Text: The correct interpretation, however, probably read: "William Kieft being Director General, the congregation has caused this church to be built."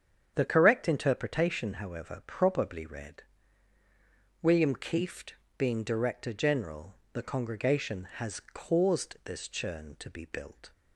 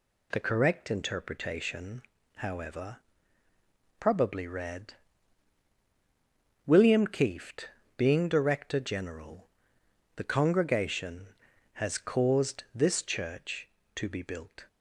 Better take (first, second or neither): second